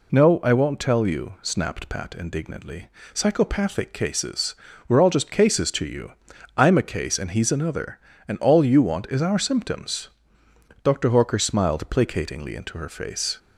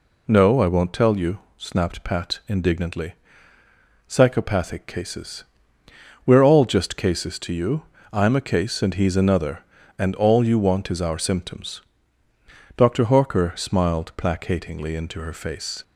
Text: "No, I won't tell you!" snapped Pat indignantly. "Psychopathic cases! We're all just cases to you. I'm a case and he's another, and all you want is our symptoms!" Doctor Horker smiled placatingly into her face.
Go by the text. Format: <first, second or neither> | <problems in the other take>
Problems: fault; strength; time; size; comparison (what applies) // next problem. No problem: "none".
neither | none